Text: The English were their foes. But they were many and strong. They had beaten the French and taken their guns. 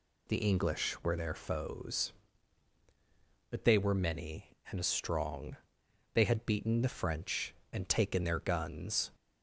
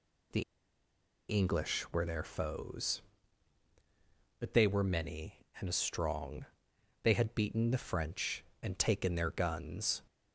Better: first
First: none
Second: pauses between "The" and "English"; noticeable; at 0.4 s; 0.88 s long

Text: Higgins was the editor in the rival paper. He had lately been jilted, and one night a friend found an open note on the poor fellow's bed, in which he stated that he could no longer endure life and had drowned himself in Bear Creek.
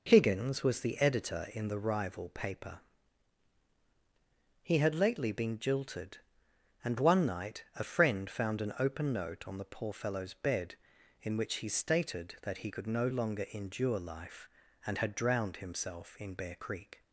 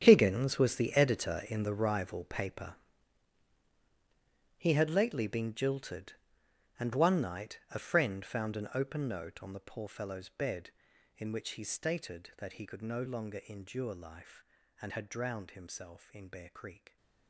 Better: first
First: none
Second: gets quieter; strong; throughout; 15 dB

